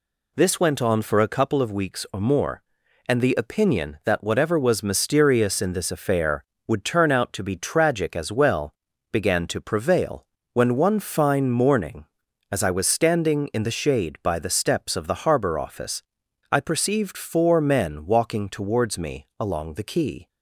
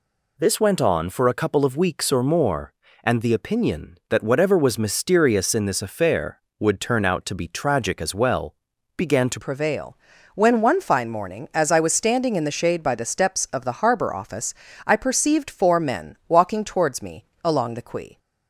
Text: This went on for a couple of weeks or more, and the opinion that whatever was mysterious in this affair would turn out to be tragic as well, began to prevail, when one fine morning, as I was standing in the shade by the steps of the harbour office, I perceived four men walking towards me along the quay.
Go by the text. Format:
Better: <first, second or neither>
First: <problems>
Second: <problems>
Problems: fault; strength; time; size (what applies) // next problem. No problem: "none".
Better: first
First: none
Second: changes voice at "prevail"; from 9.4 s on; 8.7 s long // pauses between "me" and "along"; slight; at 17.2 s; 0.18 s long